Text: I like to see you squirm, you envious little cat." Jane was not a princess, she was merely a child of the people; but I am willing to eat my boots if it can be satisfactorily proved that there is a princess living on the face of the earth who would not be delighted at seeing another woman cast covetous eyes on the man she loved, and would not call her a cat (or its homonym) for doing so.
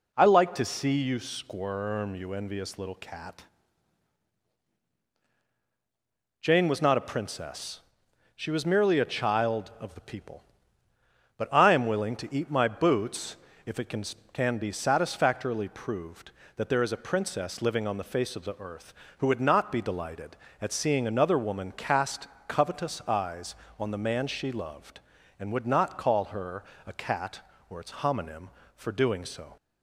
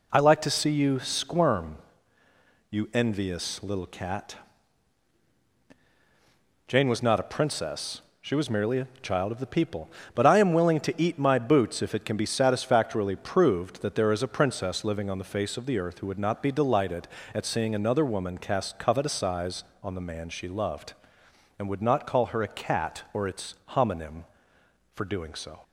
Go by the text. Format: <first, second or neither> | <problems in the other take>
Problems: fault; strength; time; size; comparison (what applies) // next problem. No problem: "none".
second | pauses between "boots" and "if"; slight; at 13.3 s; 0.28 s long // says "can" twice; at 14.3 s // pauses between "cast" and "covetous"; slight; at 22.2 s; 0.22 s long // pauses between "her" and "a"; slight; at 26.6 s; 0.20 s long